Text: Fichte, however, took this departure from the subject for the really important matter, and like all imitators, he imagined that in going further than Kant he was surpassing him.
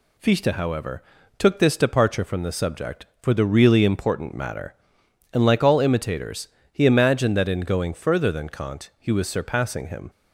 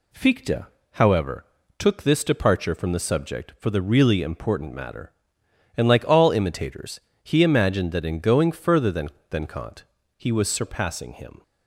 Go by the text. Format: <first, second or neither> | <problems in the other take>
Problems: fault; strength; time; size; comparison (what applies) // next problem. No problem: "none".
first | says "than" twice; at 9.3 s // pauses between "Kant" and "he"; slight; at 9.8 s; 0.32 s long